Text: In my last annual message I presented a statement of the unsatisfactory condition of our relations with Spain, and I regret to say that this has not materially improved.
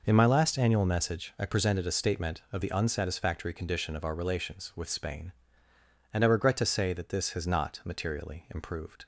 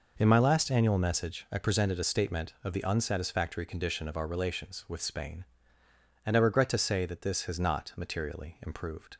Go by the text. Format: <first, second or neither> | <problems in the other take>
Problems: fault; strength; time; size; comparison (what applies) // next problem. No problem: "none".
neither | none